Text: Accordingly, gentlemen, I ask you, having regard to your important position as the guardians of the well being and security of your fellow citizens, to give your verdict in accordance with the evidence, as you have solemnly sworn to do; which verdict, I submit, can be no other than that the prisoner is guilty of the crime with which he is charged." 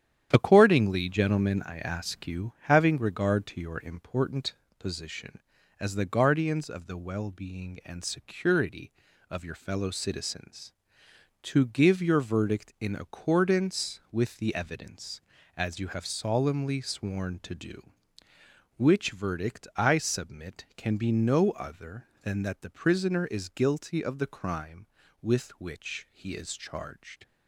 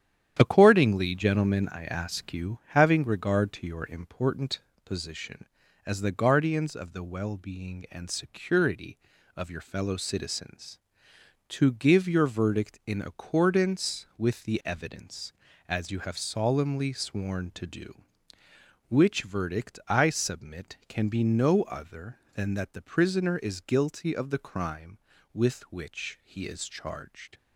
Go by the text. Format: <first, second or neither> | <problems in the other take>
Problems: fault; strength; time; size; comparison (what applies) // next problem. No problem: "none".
neither | starts louder than the rest; strong; the same in both // pauses between "important" and "position"; slight; the same in both